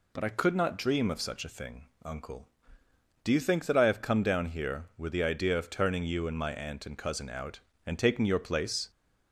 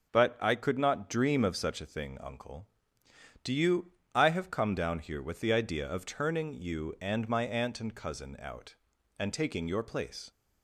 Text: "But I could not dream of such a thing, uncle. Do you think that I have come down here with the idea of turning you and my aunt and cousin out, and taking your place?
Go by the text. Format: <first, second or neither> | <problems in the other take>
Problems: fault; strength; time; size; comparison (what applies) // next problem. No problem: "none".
first | skips "think that"; at 4.0 s